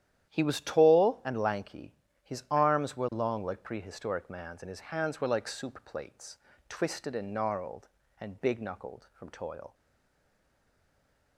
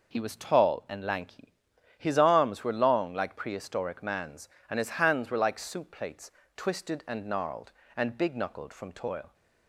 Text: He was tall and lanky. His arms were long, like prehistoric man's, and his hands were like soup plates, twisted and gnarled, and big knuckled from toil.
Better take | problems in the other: second | starts louder than the rest; strong; until 1.3 s; 11 dB // stays silent after the last word; noticeable; from 9.7 s on; 1.6 s long

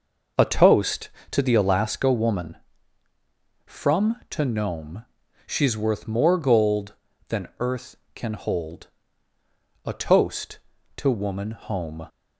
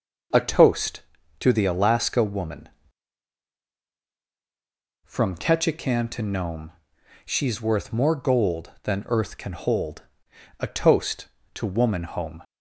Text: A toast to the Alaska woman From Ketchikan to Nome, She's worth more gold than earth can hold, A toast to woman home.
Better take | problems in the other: second | skips "Ketchikan"; at 4.2 s

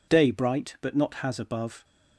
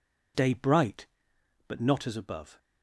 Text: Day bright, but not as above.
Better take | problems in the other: second | says "has" for "as"; at 1.1 s

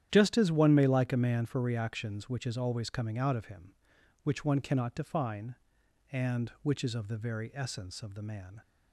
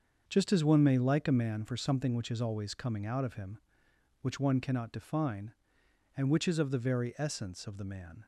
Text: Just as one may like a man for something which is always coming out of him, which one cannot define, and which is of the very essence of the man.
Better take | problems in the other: second | starts louder than the rest; strong; until 1.1 s; 10.5 dB; also in the second // says "reactions" for "something"; at 1.6 s

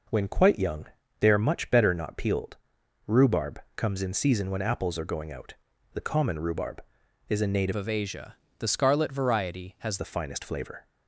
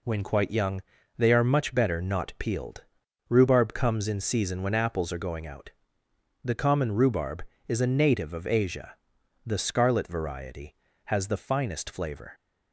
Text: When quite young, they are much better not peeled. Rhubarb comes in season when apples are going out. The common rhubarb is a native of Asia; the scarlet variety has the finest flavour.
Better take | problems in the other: second | pauses between "Rhubarb" and "comes"; slight; at 3.6 s; 0.16 s long // changes voice from "of" to "has"; from 7.7 to 9.9 s; 2.2 s long

